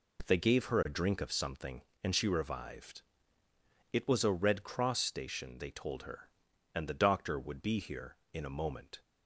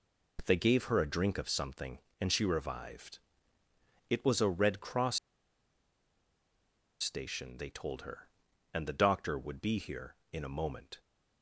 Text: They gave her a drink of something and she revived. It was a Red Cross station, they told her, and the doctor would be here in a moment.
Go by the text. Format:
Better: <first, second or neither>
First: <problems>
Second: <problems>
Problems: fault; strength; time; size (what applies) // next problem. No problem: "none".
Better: first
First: none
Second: pauses between "Cross" and "station"; strong; at 5.1 s; 1.8 s long